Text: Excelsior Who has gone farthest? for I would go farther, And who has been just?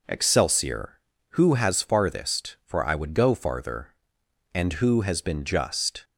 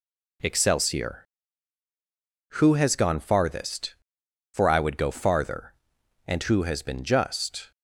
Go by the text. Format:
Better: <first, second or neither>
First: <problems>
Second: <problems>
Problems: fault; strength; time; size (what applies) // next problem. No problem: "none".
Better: second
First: skips "gone"; at 1.8 s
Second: none